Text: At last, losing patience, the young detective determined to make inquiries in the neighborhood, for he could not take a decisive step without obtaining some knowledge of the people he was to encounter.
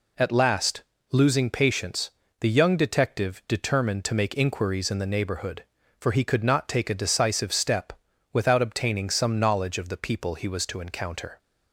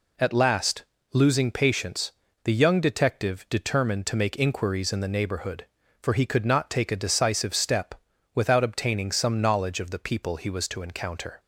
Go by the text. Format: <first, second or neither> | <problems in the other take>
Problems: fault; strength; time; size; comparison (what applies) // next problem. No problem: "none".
neither | pauses between "step" and "without"; the same in both